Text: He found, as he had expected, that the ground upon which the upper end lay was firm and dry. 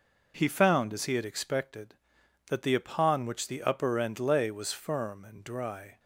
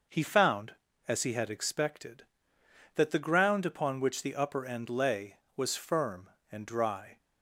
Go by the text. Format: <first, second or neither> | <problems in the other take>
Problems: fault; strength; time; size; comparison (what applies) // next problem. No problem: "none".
second | skips "ground"; at 2.7 s